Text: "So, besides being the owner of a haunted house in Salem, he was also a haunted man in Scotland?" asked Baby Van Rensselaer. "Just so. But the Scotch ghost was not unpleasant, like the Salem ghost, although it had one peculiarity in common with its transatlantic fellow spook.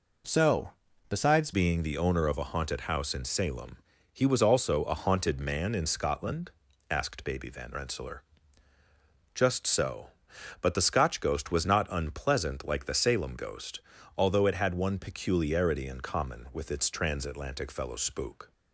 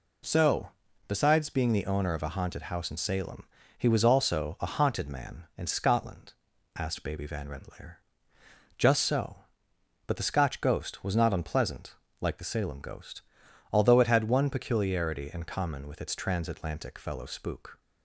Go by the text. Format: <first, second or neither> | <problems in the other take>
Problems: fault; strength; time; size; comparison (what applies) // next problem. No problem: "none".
second | changes voice at "being"; from 1.5 s on; 17.0 s long